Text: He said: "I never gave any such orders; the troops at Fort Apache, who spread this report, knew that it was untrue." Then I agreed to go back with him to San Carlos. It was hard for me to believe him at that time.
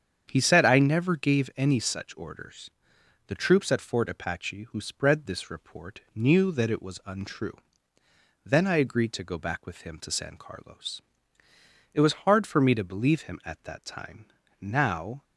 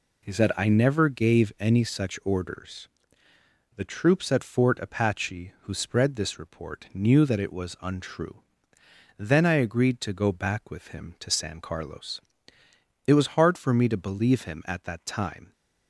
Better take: second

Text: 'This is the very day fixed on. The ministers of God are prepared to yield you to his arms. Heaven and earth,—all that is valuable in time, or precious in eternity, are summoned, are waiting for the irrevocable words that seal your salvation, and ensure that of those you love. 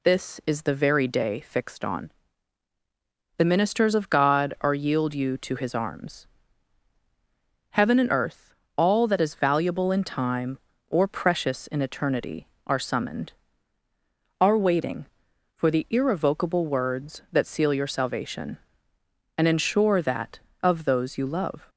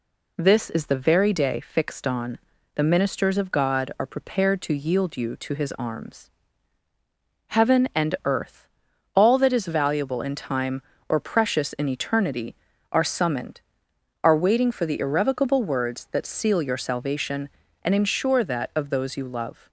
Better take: second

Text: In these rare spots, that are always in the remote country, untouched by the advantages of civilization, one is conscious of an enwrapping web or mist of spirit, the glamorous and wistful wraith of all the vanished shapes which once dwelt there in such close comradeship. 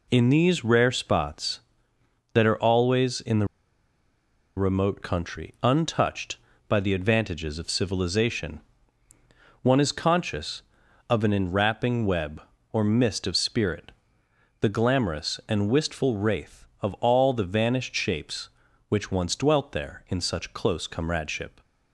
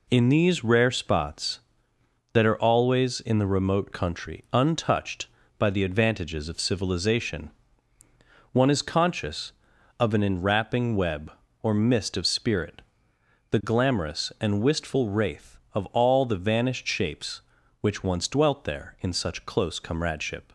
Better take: second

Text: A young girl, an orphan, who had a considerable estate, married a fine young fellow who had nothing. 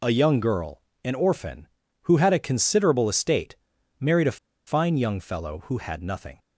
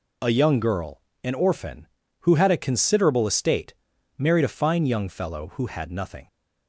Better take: second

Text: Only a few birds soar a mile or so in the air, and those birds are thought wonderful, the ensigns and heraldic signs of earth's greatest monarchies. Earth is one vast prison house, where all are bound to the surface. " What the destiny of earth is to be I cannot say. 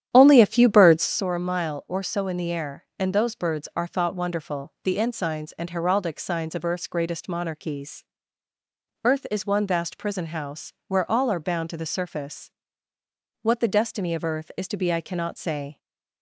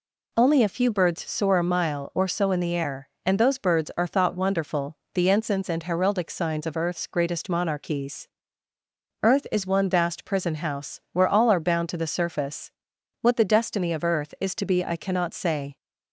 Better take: second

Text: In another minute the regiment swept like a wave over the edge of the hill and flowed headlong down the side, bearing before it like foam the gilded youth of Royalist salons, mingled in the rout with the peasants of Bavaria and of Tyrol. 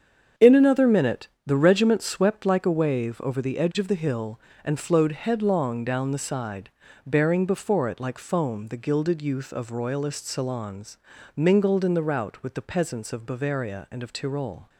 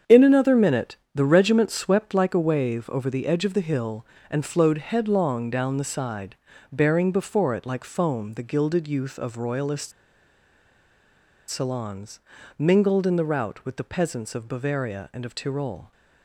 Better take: first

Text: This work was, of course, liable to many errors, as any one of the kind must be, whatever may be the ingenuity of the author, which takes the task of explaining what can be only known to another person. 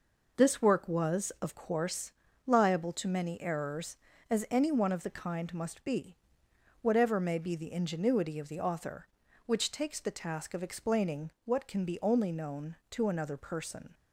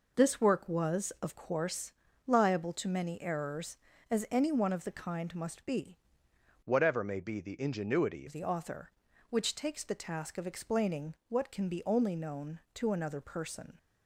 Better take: first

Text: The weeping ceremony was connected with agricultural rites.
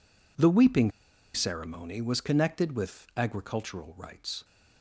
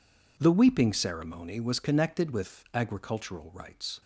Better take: second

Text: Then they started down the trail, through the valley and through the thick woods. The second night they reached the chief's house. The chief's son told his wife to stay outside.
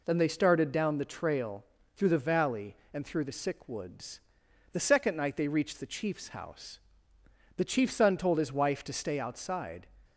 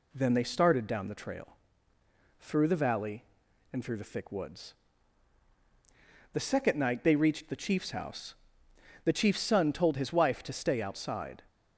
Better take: second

